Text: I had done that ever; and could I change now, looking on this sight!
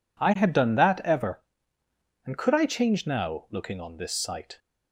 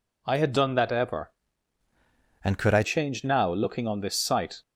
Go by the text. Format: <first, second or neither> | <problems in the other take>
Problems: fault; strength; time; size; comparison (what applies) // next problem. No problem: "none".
first | changes voice from "and" to "I"; from 2.4 to 2.8 s; 0.4 s long